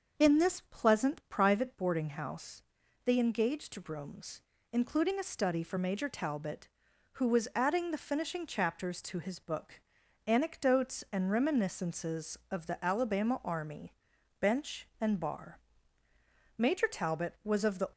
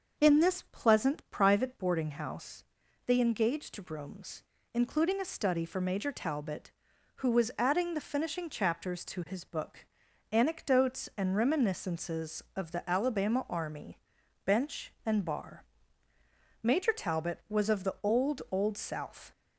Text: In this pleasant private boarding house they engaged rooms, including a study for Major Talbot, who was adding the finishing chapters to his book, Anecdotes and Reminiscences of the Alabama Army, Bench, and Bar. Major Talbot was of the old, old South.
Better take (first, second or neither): second